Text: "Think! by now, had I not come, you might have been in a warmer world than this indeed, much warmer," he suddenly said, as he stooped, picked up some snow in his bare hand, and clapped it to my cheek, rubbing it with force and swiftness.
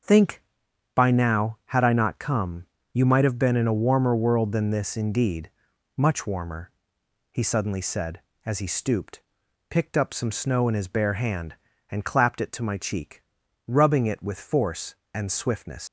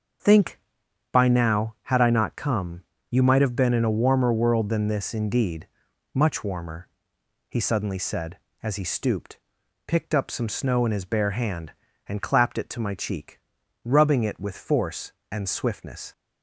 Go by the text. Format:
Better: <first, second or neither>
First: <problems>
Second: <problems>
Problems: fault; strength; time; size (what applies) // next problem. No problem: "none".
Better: second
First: starts louder than the rest; until 1.5 s; 6 dB // leaves "swiftness" unfinished; at 15.8 s; 75 ms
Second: starts louder than the rest; until 1.7 s; 6 dB